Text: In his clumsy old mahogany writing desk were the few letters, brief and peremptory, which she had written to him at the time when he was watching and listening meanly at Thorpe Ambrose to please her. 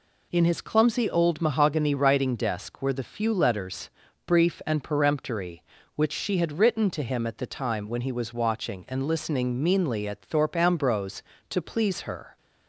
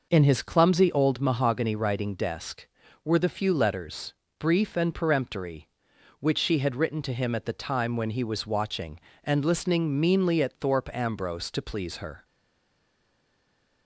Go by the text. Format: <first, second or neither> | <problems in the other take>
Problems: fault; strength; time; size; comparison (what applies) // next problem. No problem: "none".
first | stays silent after the last word; noticeable; from 12.2 s on; 1.6 s long